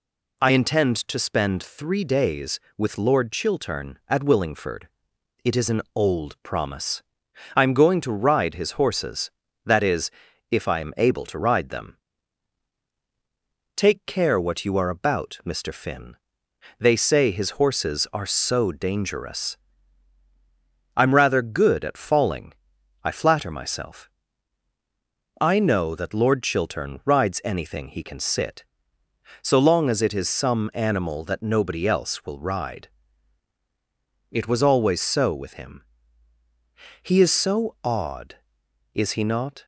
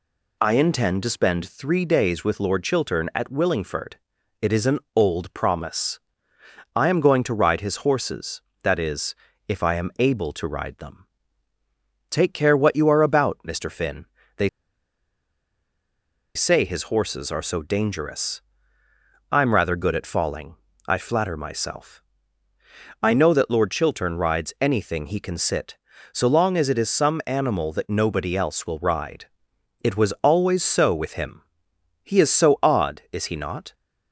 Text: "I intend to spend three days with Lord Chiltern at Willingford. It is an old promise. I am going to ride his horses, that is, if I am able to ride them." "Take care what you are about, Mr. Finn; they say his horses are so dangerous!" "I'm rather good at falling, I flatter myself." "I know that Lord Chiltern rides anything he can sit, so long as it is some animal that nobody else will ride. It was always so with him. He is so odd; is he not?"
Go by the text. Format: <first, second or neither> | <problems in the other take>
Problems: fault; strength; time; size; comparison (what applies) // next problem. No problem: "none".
first | pauses between "they" and "say"; strong; at 14.4 s; 1.8 s long